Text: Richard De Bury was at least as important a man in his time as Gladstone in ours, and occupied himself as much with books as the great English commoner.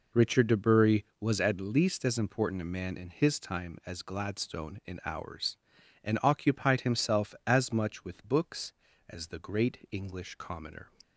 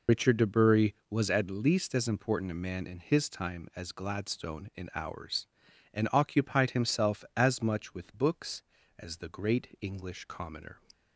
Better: first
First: none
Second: loses the start of "Richard"; at 0.0 s; 45 ms

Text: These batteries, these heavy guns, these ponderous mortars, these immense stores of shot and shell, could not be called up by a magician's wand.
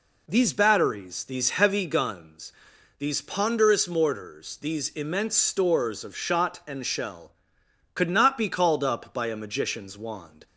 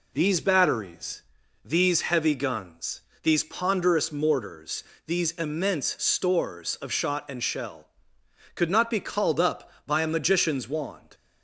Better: neither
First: none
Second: none

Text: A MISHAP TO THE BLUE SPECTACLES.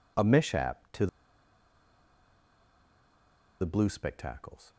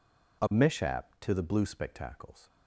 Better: second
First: pauses between "TO" and "THE"; strong; at 1.0 s; 2.5 s long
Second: none

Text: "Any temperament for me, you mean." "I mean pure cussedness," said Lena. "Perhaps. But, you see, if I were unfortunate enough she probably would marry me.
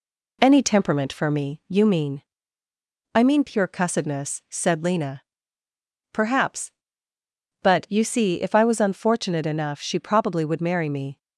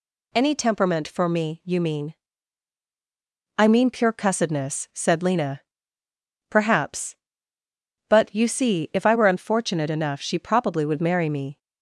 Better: second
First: says "was" for "were"; at 8.6 s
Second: none

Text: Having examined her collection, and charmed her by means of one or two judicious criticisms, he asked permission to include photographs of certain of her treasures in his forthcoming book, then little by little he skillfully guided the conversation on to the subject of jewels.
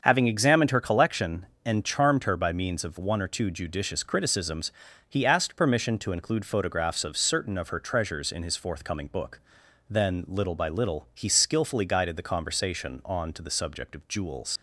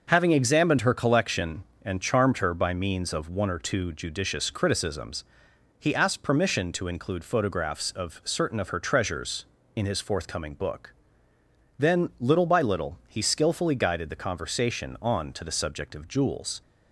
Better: second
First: starts louder than the rest; until 1.0 s; 7 dB // leaves "jewels" unfinished; at 14.5 s; 70 ms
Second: starts louder than the rest; until 1.1 s; 6.5 dB

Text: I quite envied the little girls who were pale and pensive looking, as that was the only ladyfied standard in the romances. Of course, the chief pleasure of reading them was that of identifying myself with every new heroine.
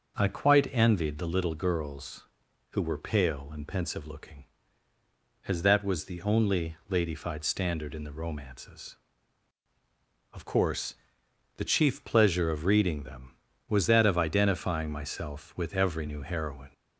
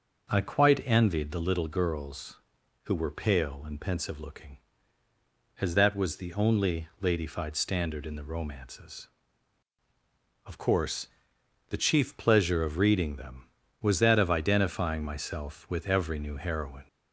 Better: neither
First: none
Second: none

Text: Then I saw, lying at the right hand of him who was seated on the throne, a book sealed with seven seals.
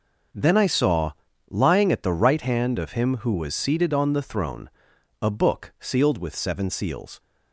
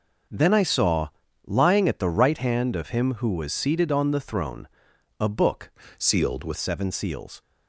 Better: first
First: none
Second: changes voice from "sealed" to "with"; from 5.9 to 6.5 s; 0.6 s long

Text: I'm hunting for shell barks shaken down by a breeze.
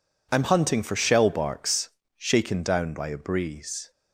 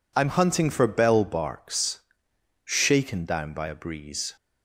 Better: first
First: pauses between "barks" and "shaken"; slight; at 1.8 s; 0.28 s long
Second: says "bell" for "shell"; at 0.8 s // pauses between "barks" and "shaken"; noticeable; at 1.9 s; 0.66 s long

